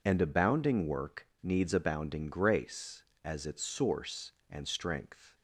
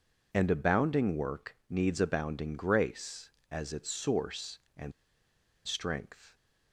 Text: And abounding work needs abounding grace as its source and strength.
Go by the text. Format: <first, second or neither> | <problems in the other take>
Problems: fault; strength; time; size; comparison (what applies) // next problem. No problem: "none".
first | pauses between "and" and "strength"; noticeable; at 4.9 s; 0.74 s long